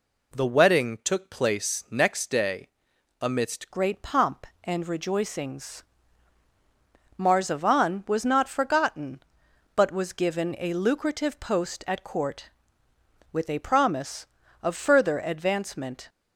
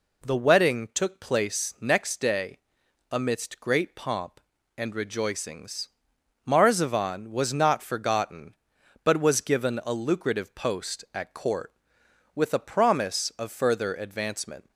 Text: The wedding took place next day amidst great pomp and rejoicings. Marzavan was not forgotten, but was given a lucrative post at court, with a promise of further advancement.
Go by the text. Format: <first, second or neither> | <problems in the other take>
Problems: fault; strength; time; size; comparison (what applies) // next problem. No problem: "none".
second | pauses between "day" and "amidst"; noticeable; at 2.6 s; 0.50 s long; noticeable in the second // changes voice at "great"; from 3.7 s on; 12.3 s long